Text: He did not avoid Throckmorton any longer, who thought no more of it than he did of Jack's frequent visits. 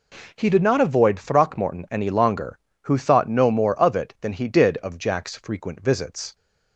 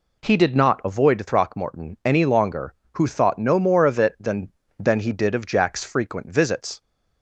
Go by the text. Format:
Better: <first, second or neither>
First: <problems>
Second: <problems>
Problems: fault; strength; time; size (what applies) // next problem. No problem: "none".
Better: first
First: none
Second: says "than" twice; at 4.7 s